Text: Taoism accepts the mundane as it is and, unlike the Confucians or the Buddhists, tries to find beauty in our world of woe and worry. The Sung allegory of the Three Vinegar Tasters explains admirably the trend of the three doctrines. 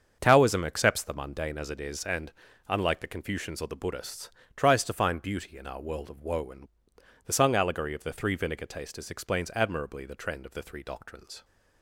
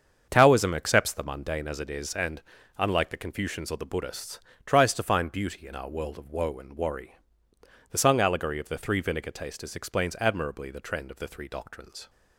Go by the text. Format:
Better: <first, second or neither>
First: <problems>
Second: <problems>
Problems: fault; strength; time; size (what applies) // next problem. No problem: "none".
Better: second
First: starts louder than the rest; until 1.2 s; 7 dB // skips "worry"; at 6.9 s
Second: starts louder than the rest; until 1.2 s; 7 dB